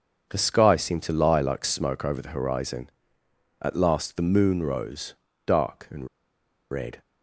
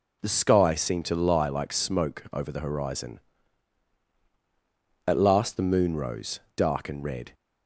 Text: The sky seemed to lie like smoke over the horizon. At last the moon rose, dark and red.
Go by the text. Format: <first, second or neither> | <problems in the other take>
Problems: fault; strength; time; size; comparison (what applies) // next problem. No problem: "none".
second | pauses between "and" and "red"; noticeable; at 6.0 s; 0.65 s long